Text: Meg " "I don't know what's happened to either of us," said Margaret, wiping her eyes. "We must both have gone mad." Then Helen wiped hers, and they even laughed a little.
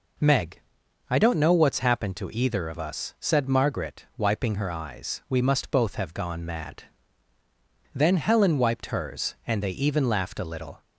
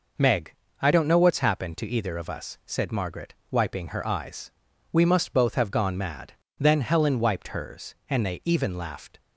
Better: first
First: none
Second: stops before "a little"; at 9.1 s

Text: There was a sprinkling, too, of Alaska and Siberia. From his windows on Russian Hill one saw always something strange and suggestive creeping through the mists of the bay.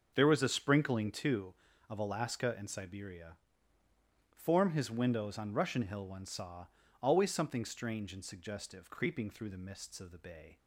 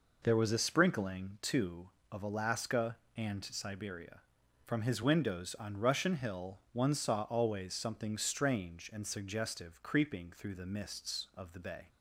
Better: second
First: says "Form" for "From"; at 4.3 s // pauses between "saw" and "always"; slight; at 6.6 s; 0.34 s long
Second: none

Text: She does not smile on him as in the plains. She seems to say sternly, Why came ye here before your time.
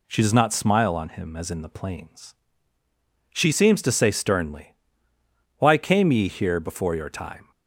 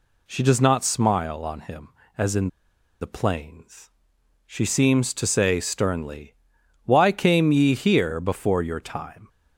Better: first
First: none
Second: pauses between "in" and "the"; noticeable; at 2.4 s; 0.52 s long

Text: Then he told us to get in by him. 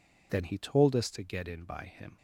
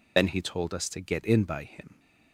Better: first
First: none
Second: loses the start of "Then"; at 0.1 s; 50 ms

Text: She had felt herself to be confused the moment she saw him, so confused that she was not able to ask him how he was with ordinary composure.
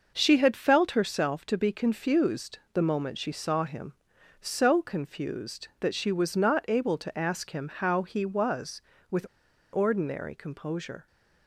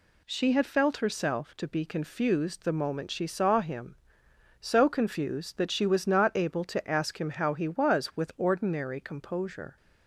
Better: second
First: starts louder than the rest; noticeable; until 1.1 s; 6 dB // pauses between "with" and "ordinary"; noticeable; at 9.2 s; 0.47 s long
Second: none

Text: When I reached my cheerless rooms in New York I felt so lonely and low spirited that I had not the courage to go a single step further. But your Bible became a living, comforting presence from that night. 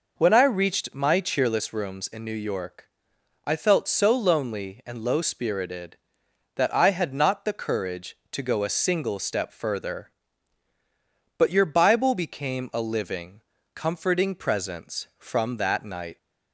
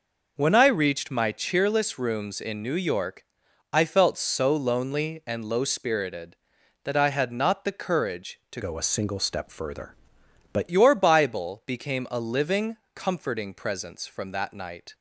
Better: first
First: pauses between "York" and "I"; noticeable; at 2.8 s; 0.58 s long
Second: pauses between "York" and "I"; noticeable; at 3.2 s; 0.48 s long // changes voice from "go" to "But"; from 8.6 to 10.6 s; 2.0 s long

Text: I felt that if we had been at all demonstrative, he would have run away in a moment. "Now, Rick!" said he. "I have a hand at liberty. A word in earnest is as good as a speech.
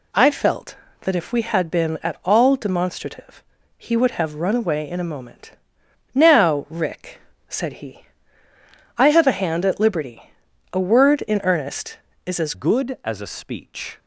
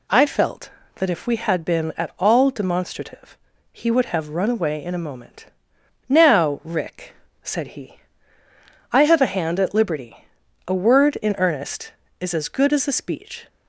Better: second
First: changes voice at "good"; from 12.5 s on; 1.4 s long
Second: none

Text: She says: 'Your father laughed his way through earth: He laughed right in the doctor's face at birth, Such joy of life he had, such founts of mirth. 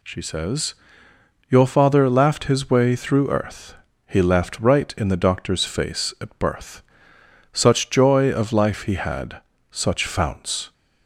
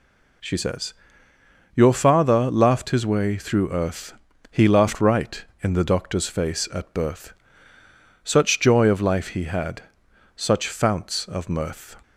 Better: second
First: stops before "of mirth"; at 10.7 s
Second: none

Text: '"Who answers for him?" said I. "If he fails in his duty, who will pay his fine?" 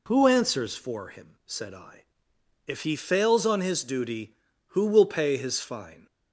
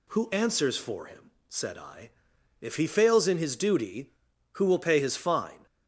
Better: second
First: says "on" for "in"; at 3.4 s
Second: none

